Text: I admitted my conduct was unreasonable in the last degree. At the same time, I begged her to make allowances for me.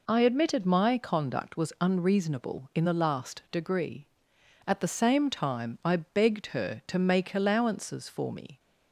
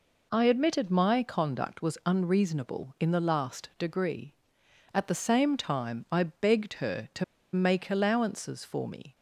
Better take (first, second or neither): first